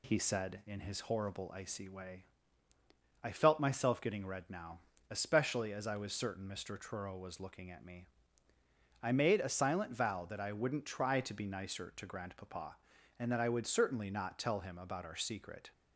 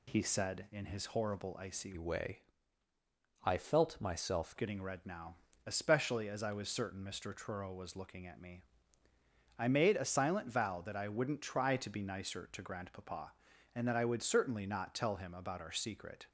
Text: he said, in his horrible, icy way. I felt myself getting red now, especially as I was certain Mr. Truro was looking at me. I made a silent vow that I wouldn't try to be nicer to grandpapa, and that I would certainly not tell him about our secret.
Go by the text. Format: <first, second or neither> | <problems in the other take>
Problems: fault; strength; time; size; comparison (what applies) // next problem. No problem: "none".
first | changes voice from "way" to "myself"; from 1.9 to 4.5 s; 2.6 s long